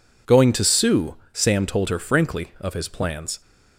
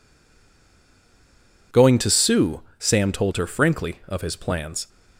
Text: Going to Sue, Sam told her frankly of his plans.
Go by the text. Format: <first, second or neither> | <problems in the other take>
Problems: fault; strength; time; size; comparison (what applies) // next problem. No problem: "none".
first | stays silent before the first word; noticeable; until 1.7 s; 1.7 s long